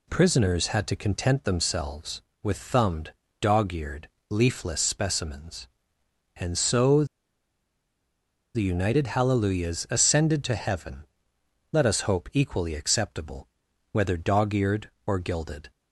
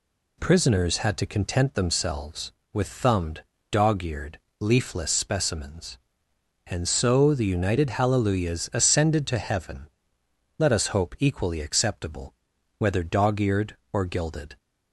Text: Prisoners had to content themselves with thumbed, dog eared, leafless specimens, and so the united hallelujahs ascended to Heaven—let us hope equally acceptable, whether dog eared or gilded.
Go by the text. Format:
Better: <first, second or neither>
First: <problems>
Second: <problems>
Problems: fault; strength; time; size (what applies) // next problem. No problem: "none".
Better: second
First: pauses between "so" and "the"; strong; at 7.0 s; 1.5 s long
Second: none